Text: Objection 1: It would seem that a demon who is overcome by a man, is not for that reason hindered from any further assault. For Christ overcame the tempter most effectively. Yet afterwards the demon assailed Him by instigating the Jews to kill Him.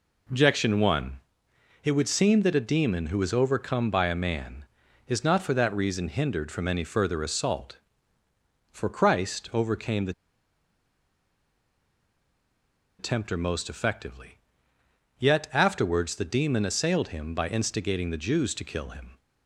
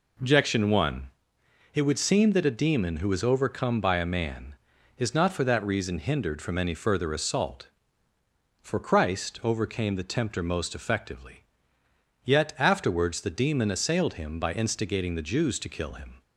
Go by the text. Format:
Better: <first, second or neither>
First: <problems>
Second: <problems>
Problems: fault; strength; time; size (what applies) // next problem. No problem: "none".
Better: second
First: pauses between "the" and "tempter"; strong; at 10.1 s; 2.8 s long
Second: none